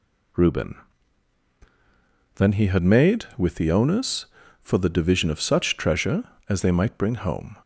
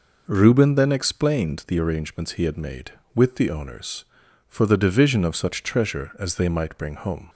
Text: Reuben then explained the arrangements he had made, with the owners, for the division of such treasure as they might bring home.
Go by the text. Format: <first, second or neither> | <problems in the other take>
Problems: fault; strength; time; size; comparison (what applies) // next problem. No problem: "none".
second | pauses between "Reuben" and "then"; strong; at 0.7 s; 1.6 s long // skips "explained the arrangements"; at 2.5 s